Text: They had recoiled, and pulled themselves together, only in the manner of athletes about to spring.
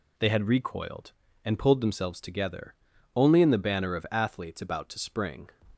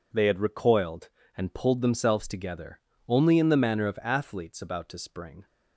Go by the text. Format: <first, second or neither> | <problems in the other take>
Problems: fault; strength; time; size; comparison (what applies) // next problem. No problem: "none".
second | says "banner" for "manner"; at 3.5 s